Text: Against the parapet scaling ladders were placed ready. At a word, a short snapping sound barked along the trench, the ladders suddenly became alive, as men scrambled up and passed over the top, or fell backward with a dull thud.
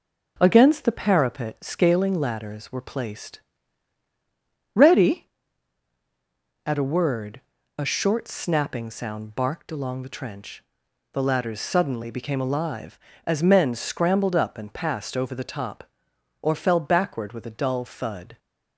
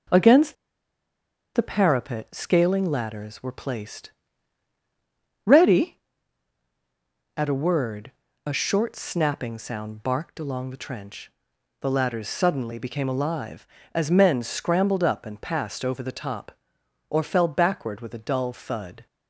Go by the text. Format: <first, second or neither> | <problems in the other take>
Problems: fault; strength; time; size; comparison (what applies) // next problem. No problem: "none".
first | pauses between "Against" and "the"; at 0.5 s; 1.0 s long // pauses between "placed" and "ready"; strong; at 4.0 s; 1.3 s long; strong in the first